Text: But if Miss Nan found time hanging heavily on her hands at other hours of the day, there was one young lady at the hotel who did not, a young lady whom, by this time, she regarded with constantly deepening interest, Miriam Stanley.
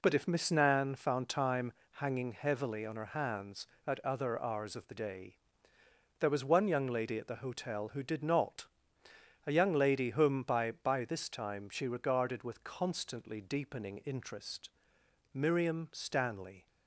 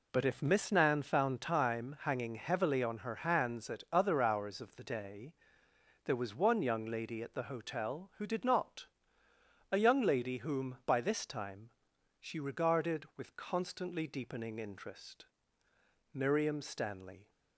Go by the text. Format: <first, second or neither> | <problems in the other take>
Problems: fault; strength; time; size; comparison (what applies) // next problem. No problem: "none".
second | pauses between "time" and "hanging"; slight; at 1.7 s; 0.20 s long // says "by" twice; at 10.7 s